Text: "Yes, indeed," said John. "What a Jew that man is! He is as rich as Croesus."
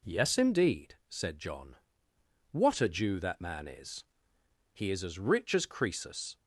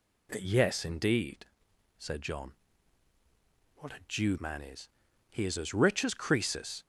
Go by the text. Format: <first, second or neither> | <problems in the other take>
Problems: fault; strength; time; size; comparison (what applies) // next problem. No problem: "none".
first | skips "that"; at 4.3 s